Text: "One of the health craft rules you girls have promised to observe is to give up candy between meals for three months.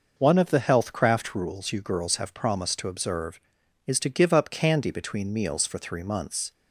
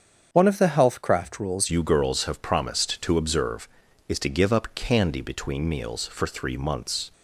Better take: first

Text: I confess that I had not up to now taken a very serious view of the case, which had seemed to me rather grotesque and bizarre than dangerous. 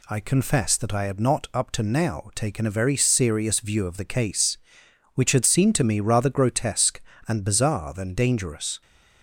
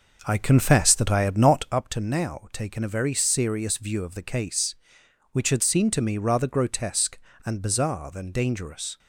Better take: first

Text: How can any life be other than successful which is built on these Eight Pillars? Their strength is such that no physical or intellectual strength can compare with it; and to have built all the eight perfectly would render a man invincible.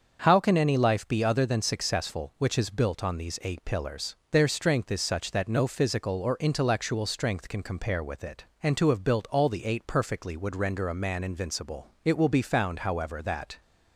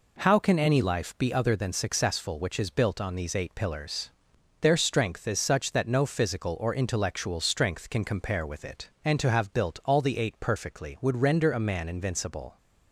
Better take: second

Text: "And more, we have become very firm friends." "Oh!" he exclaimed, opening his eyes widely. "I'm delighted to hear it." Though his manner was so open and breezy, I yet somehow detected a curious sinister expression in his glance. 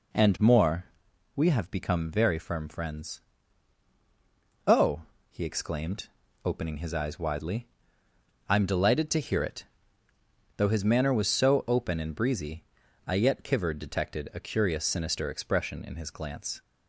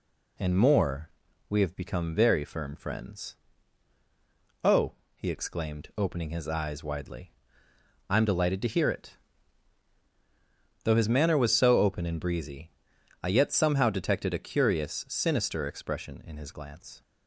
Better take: second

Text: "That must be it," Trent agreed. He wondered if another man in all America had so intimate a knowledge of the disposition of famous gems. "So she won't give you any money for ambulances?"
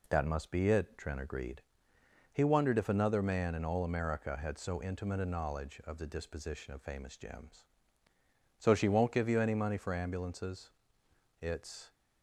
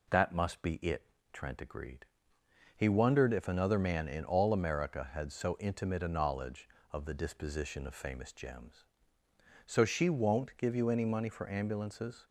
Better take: second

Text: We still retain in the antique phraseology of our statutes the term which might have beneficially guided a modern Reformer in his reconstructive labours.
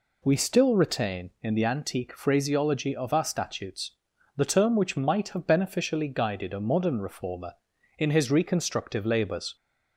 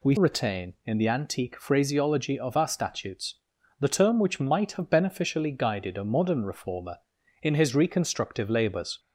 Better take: first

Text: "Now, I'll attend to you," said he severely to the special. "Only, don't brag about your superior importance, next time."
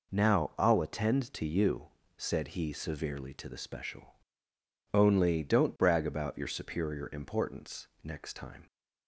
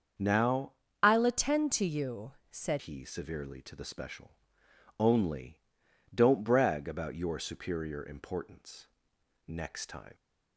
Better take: first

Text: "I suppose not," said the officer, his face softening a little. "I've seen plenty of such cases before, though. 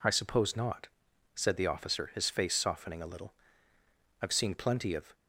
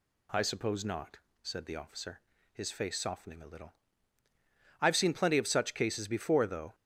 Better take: second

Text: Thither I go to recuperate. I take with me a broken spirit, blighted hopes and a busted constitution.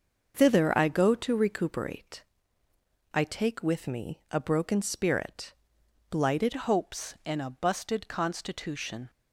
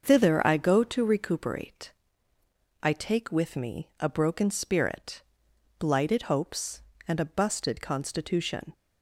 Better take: second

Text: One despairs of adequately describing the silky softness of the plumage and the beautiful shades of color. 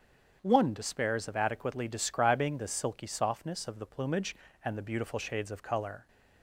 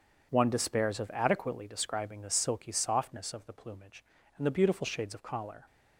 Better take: first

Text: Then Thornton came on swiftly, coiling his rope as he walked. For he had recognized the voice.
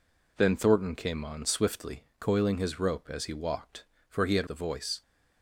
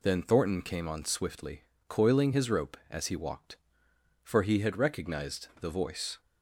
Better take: second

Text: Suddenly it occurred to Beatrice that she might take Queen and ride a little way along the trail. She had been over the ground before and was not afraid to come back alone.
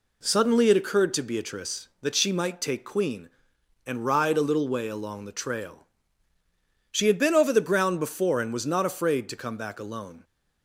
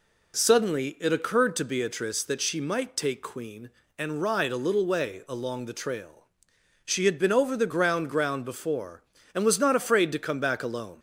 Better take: first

